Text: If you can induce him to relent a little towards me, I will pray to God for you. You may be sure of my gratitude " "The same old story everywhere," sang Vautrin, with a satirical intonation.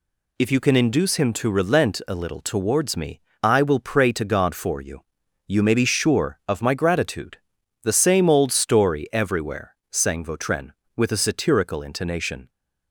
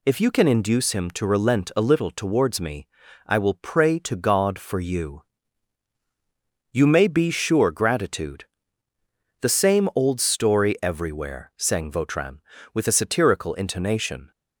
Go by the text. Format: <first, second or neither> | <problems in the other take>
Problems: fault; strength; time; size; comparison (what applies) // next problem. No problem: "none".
first | skips "of my"; at 7.7 s